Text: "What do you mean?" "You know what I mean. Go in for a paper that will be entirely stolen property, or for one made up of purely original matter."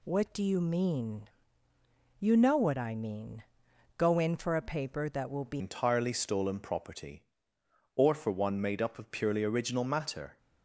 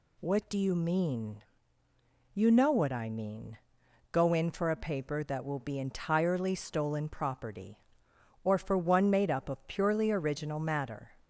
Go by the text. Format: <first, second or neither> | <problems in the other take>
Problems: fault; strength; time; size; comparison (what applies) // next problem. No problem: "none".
second | changes voice at "entirely"; from 5.5 s on; 4.8 s long